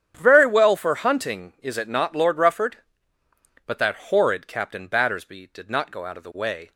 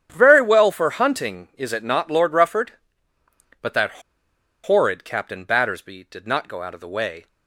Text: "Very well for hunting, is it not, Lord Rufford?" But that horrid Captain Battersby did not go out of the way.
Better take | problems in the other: first | starts louder than the rest; strong; until 1.1 s; 9 dB; strong in the first // pauses between "that" and "horrid"; noticeable; at 4.0 s; 0.62 s long

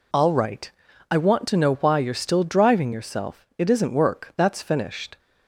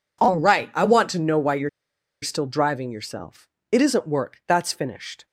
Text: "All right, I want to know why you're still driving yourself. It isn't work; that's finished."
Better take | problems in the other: first | pauses between "you're" and "still"; noticeable; at 1.6 s; 0.52 s long

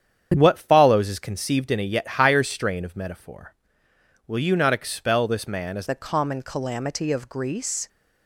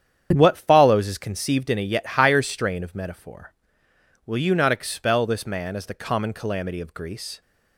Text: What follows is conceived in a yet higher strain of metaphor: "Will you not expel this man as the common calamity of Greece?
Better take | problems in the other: second | starts louder than the rest; strong; until 1.3 s; 8.5 dB; strong in the second // changes voice at "the"; from 5.8 s on; 2.0 s long

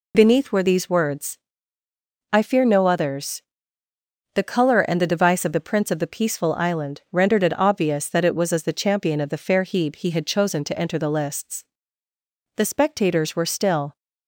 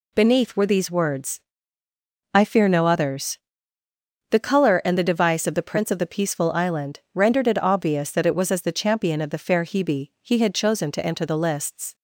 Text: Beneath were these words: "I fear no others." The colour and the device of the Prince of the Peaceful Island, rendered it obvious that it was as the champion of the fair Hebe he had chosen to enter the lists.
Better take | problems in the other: second | goes on to say "The spectators were still"; from 12.5 s on; 1.4 s long

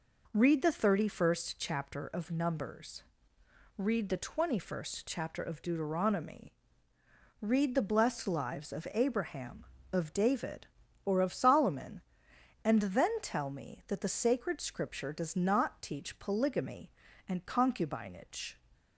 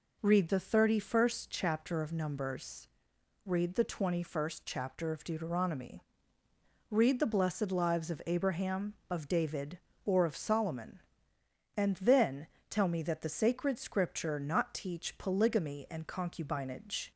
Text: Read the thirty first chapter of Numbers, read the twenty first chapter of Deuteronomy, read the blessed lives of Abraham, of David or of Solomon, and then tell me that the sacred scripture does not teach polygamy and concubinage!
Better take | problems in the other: first | pauses between "then" and "tell"; slight; at 12.4 s; 0.22 s long // skips "does"; at 14.4 s

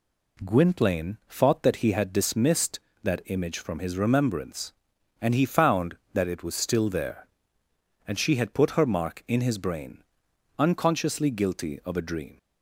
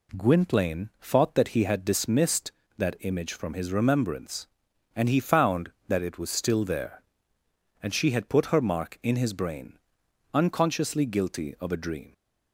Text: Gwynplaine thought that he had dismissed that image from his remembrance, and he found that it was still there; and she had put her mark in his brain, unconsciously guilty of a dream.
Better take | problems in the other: neither | none

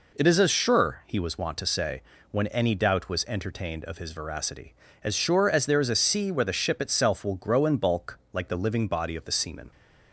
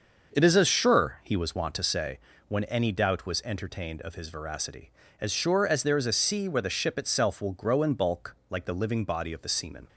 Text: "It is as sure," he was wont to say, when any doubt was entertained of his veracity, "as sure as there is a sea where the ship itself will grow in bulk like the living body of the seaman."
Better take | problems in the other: first | starts louder than the rest; until 2.1 s; 6 dB

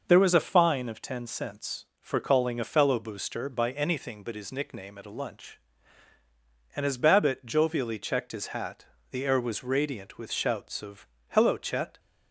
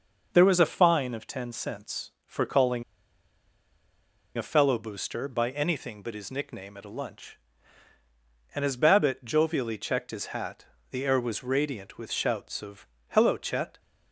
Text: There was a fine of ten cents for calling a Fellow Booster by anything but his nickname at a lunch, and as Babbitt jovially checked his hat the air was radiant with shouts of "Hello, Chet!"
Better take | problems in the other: first | pauses between "calling" and "a"; strong; at 2.8 s; 1.5 s long // pauses between "hat" and "the"; slight; at 10.6 s; 0.26 s long; slight in the first // pauses between "of" and "Hello"; slight; at 12.8 s; 0.22 s long; slight in the first

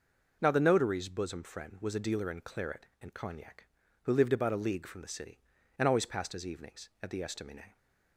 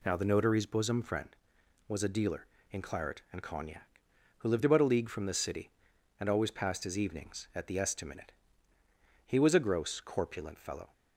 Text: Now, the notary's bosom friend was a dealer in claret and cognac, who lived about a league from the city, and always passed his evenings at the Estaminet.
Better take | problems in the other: first | goes on to say "He was a gross corpulent fellow"; from 9.2 s on; 1.6 s long

